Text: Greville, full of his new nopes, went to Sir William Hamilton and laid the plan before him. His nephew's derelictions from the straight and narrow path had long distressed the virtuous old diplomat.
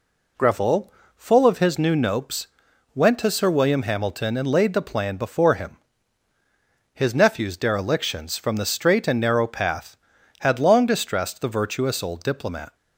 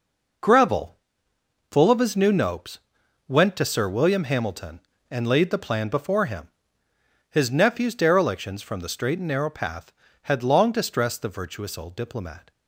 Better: neither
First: none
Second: none

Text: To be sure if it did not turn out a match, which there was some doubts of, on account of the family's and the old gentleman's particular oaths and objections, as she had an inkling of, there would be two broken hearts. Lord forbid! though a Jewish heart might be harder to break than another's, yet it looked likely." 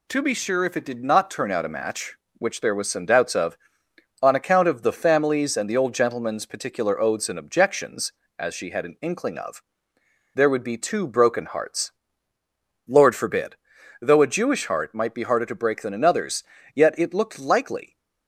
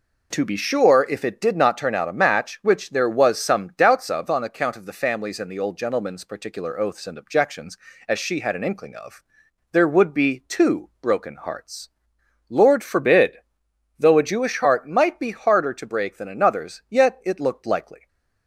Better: neither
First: none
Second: none

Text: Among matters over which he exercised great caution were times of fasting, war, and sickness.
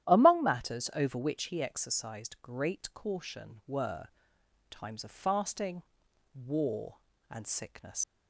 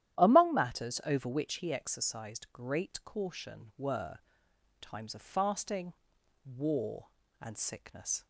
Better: second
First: starts louder than the rest; strong; until 1.1 s; 11.5 dB // pauses between "were" and "times"; noticeable; at 4.0 s; 0.60 s long // leaves "sickness" unfinished; at 8.0 s; 110 ms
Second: starts louder than the rest; strong; until 1.2 s; 12 dB // pauses between "were" and "times"; noticeable; at 4.1 s; 0.60 s long

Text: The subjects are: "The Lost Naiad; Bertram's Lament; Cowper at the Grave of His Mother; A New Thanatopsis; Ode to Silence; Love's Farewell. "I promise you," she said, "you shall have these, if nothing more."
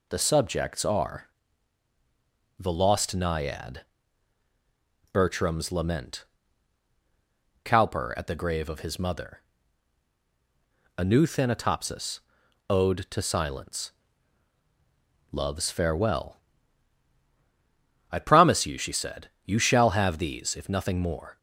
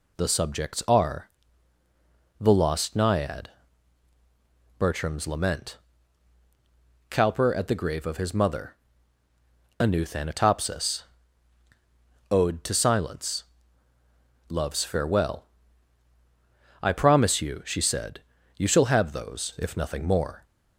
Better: first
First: none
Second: says "those" for "these"; at 19.1 s

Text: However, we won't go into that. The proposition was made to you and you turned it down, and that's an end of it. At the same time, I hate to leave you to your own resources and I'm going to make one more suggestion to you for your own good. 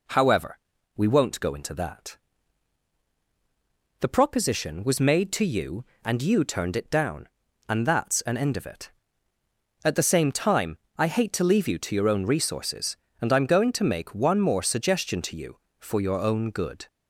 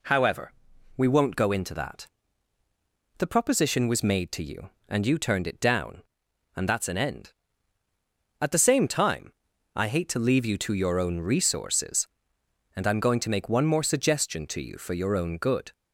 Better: first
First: none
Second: skips "of it"; at 7.8 s

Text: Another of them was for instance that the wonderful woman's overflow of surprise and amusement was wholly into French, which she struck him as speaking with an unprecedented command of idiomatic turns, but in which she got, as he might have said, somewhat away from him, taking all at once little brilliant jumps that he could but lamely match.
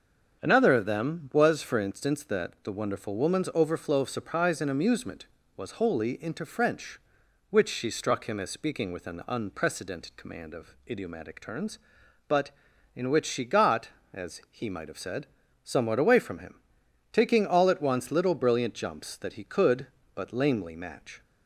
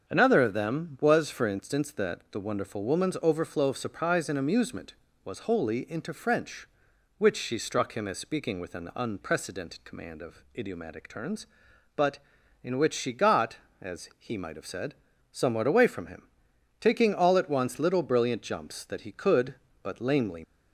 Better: first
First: starts louder than the rest; until 1.4 s; 7 dB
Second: starts louder than the rest; until 1.1 s; 7 dB // stops before "match"; at 20.4 s

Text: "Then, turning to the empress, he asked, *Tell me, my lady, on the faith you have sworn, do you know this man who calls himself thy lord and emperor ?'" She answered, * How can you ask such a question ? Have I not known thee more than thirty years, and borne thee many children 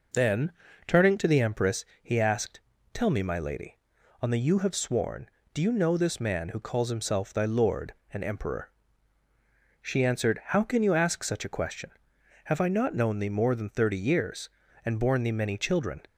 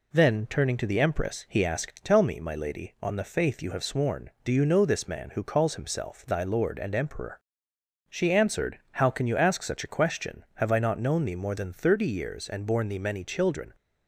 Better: second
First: starts louder than the rest; until 1.5 s; 6 dB // skips "faith"; at 4.3 s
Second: none

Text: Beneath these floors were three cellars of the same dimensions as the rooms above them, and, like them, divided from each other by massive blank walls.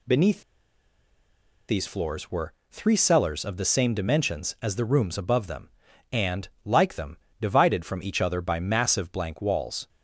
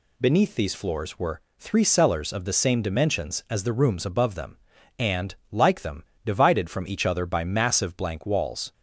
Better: second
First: pauses between "Beneath" and "these"; strong; at 0.4 s; 1.2 s long // pauses between "were" and "three"; slight; at 2.5 s; 0.16 s long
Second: pauses between "were" and "three"; slight; at 1.4 s; 0.16 s long

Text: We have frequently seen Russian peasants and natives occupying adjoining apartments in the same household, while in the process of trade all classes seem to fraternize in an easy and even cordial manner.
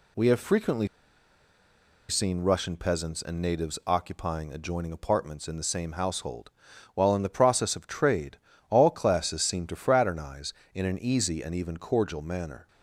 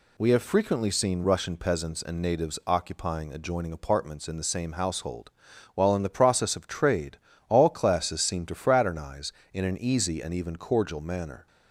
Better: second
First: pauses between "frequently" and "seen"; at 0.8 s; 1.2 s long // pauses between "trade" and "all"; slight; at 8.3 s; 0.32 s long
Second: pauses between "trade" and "all"; slight; at 7.1 s; 0.30 s long

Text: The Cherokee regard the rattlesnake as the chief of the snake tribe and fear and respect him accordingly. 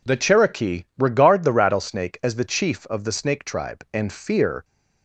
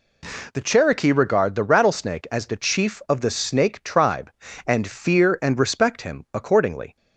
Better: second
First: stops before "and respect him accordingly"; at 4.6 s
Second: none

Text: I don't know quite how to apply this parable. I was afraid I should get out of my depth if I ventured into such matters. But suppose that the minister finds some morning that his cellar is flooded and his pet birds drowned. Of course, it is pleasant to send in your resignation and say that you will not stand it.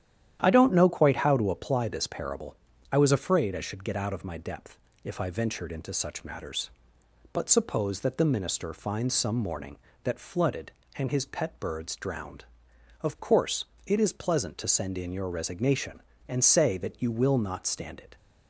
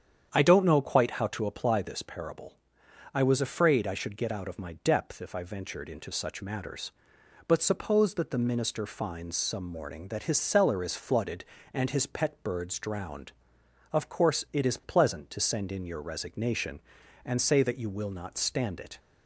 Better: second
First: starts louder than the rest; strong; until 1.4 s; 10.5 dB // pauses between "depth" and "if"; slight; at 4.7 s; 0.26 s long // skips "his cellar is"; at 10.1 s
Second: starts louder than the rest; strong; until 1.3 s; 8.5 dB

